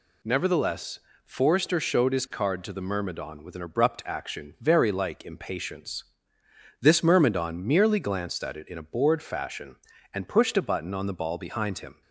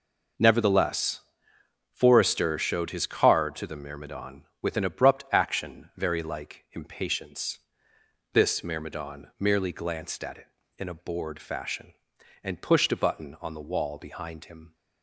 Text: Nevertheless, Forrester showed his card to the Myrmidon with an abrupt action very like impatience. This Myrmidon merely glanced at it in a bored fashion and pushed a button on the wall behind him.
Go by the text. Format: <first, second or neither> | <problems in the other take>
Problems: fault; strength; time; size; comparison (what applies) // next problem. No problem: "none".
second | says "ball" for "wall"; at 11.1 s